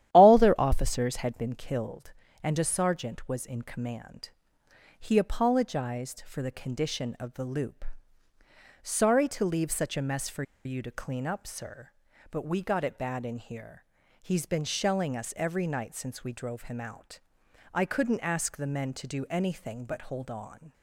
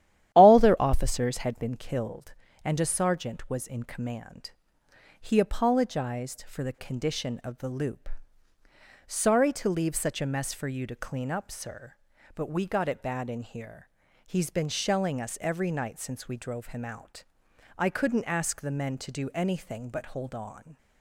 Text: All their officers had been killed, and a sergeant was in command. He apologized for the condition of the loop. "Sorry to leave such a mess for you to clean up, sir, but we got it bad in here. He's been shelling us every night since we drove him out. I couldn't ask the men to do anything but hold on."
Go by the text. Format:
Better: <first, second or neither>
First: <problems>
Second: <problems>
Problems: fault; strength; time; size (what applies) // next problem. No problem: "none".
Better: second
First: starts louder than the rest; strong; until 1.1 s; 12 dB // pauses between "for" and "you"; slight; at 10.4 s; 0.22 s long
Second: starts louder than the rest; strong; until 1.3 s; 11.5 dB